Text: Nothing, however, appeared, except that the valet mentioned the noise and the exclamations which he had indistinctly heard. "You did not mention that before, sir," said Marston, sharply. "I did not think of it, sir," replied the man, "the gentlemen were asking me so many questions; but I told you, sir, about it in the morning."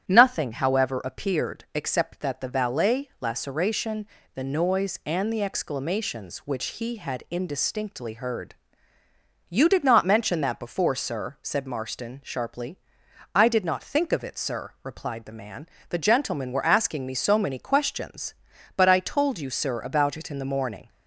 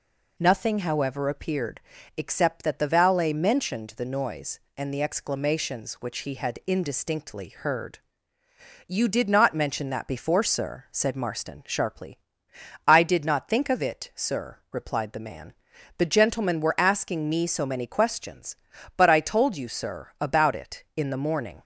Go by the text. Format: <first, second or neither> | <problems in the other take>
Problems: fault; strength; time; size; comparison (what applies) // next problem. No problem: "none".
second | starts louder than the rest; strong; until 1.1 s; 10 dB // says "laceration" for "mentioned"; at 3.1 s